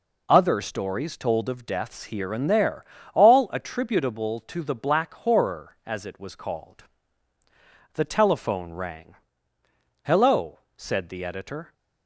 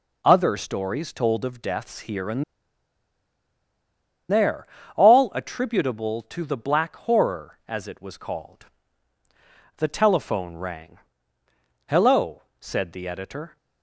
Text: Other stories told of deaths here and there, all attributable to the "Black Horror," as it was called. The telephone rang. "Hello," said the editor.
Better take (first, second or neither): first